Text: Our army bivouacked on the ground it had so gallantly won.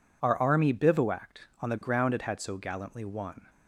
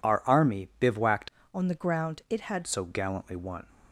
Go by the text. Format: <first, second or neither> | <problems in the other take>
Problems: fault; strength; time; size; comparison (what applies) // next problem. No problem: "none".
first | changes voice from "on" to "had"; from 1.5 to 2.6 s; 1.1 s long